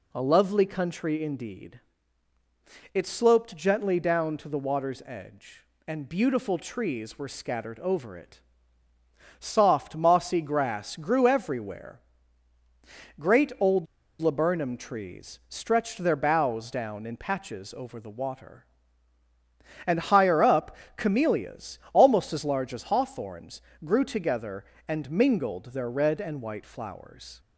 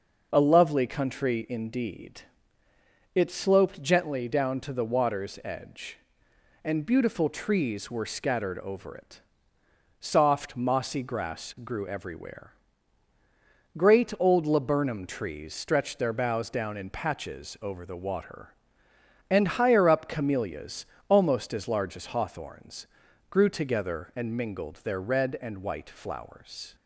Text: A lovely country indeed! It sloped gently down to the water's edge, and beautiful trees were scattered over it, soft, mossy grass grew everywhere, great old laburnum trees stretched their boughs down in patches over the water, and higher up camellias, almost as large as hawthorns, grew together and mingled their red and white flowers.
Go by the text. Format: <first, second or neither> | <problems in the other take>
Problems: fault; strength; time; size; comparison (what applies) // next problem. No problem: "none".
second | pauses between "old" and "laburnum"; slight; at 13.8 s; 0.33 s long // pauses between "up" and "camellias"; slight; at 20.7 s; 0.22 s long